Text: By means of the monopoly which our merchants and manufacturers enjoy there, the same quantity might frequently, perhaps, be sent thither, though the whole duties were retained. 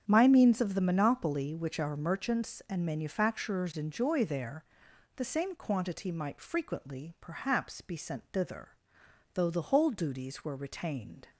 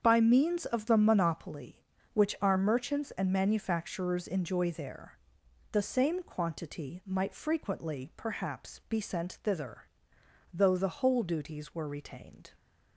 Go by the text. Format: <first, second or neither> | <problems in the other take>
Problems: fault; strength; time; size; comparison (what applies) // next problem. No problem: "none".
second | starts louder than the rest; strong; until 1.0 s; 8 dB; strong in the second // says "My" for "By"; at 0.0 s